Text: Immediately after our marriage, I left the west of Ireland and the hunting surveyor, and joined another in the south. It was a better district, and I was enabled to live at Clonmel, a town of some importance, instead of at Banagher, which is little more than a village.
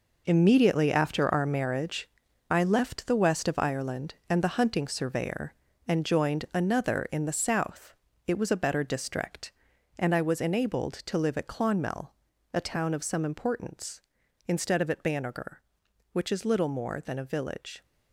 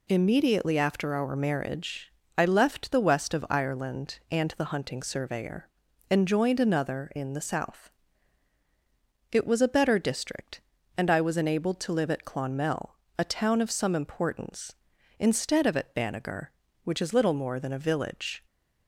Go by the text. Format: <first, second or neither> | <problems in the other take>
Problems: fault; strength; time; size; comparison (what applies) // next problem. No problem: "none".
second | gets quieter; strong; throughout; 10 dB